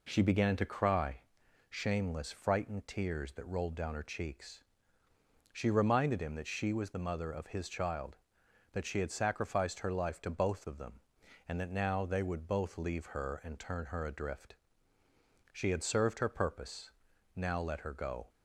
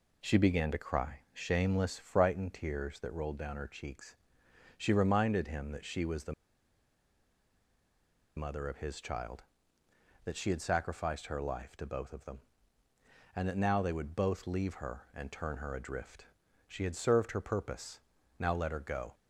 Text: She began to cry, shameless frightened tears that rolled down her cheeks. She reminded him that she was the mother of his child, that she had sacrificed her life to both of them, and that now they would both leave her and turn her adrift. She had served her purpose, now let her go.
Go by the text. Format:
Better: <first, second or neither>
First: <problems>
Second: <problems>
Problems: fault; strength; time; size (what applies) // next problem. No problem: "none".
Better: first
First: none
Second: pauses between "the" and "mother"; strong; at 6.3 s; 2.0 s long